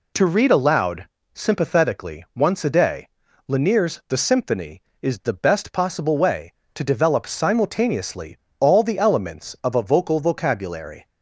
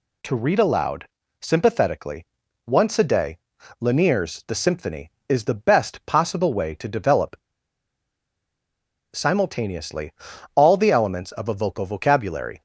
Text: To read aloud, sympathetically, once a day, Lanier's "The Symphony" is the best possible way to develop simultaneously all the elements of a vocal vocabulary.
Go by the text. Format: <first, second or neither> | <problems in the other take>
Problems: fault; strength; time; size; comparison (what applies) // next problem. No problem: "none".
first | pauses between "develop" and "simultaneously"; strong; at 7.3 s; 1.7 s long // pauses between "simultaneously" and "all"; at 10.1 s; 0.40 s long; slight in the first